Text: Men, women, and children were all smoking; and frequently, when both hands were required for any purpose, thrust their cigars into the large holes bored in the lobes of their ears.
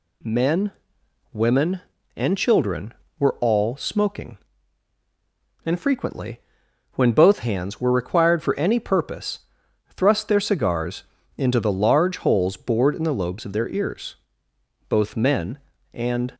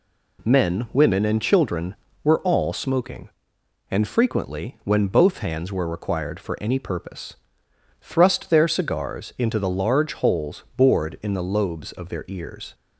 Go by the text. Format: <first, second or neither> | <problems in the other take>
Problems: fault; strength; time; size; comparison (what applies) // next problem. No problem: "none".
second | pauses between "cigars" and "into"; slight; at 11.0 s; 0.34 s long // goes on to say "Both men and"; from 14.8 s on; 1.4 s long